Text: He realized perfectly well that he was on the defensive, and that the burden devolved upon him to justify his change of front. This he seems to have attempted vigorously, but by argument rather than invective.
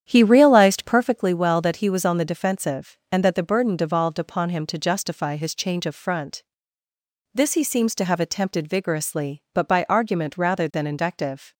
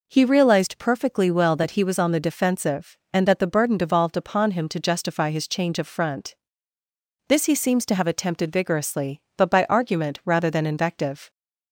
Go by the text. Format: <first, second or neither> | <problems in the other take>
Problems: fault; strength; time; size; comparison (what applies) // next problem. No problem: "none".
second | starts louder than the rest; strong; until 1.2 s; 9 dB